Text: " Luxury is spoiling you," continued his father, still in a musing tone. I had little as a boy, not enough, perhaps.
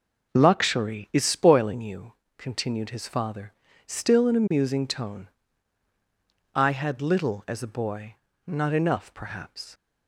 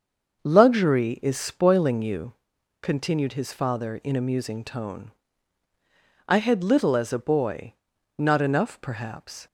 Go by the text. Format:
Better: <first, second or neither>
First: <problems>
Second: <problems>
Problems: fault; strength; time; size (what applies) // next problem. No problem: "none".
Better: first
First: none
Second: starts louder than the rest; until 1.4 s; 6 dB // skips "still"; at 4.0 s